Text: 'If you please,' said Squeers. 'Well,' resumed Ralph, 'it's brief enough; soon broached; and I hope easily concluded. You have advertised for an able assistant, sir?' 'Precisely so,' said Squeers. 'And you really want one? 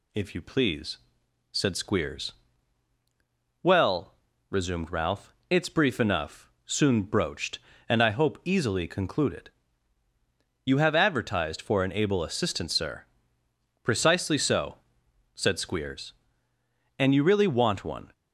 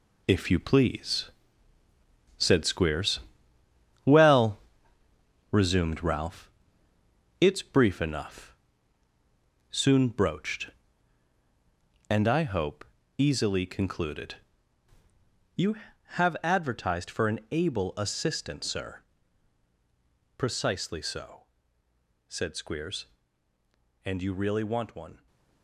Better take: first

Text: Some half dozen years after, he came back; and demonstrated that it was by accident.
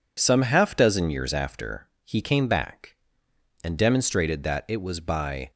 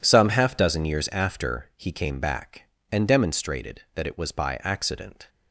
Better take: second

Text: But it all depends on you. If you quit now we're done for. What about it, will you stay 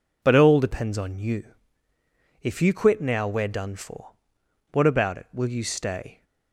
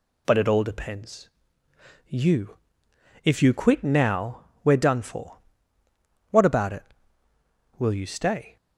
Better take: first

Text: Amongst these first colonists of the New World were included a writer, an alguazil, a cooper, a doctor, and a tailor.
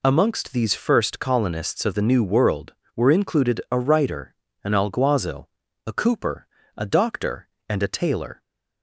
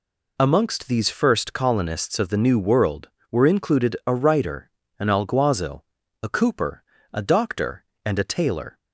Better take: neither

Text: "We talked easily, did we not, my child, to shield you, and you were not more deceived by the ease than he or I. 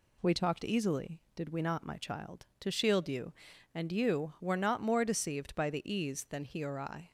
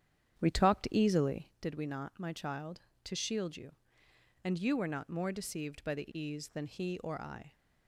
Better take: first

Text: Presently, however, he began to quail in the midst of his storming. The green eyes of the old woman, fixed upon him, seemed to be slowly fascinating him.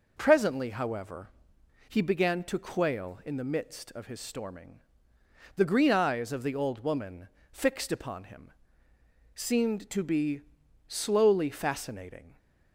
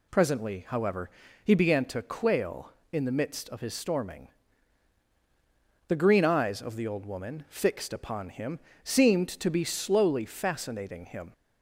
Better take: second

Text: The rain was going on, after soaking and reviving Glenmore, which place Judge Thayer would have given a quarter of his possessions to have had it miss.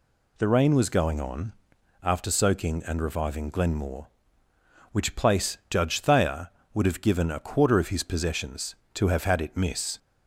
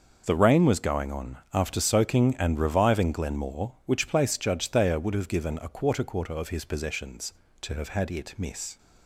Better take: first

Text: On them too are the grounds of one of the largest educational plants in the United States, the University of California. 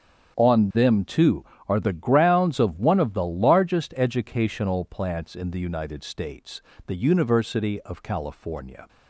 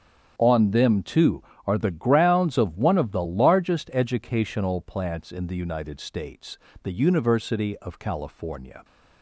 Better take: neither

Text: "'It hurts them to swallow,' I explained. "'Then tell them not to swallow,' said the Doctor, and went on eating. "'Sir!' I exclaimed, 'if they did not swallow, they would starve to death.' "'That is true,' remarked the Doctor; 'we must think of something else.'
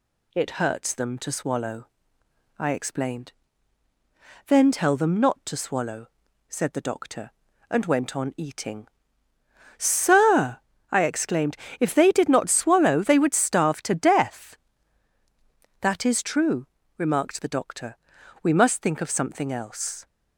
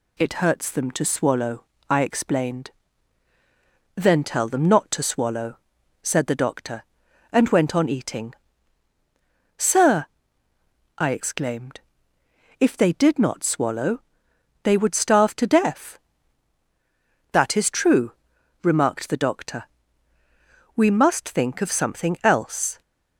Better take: neither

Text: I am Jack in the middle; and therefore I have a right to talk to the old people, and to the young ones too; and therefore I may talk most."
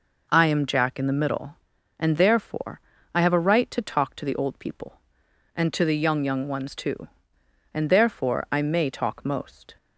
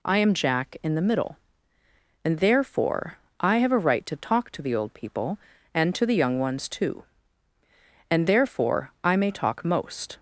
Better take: second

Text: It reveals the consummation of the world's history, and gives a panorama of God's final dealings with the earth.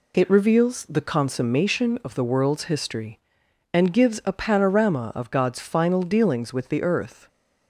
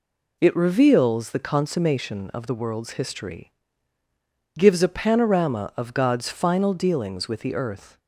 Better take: first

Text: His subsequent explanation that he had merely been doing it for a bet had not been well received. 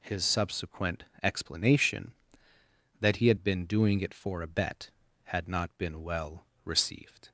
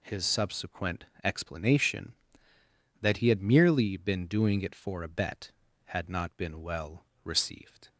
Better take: second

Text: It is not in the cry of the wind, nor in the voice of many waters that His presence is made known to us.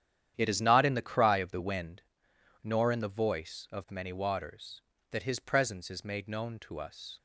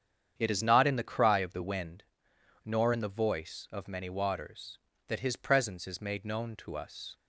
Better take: second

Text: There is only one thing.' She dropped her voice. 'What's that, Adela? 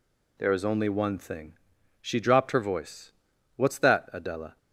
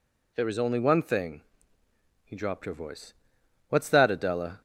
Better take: first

